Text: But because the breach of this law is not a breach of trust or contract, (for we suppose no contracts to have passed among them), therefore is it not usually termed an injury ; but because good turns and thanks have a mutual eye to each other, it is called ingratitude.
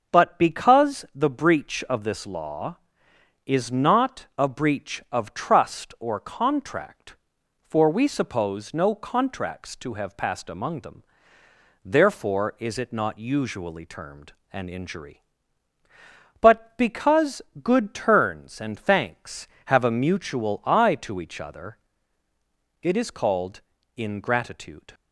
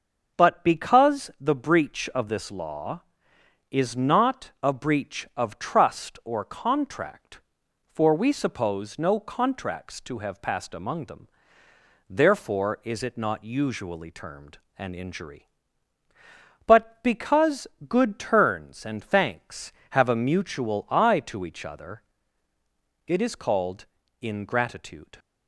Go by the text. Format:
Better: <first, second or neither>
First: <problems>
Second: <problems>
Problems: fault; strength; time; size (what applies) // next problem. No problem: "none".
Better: neither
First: starts louder than the rest; noticeable; until 1.2 s; 6 dB // pauses between "termed" and "an"; slight; at 14.3 s; 0.18 s long // pauses between "because" and "good"; slight; at 17.4 s; 0.20 s long // pauses between "called" and "ingratitude"; at 23.5 s; 0.38 s long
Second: starts louder than the rest; until 1.4 s; 6 dB // pauses between "termed" and "an"; slight; at 14.5 s; 0.18 s long // pauses between "because" and "good"; slight; at 17.6 s; 0.20 s long // pauses between "called" and "ingratitude"; at 23.8 s; 0.38 s long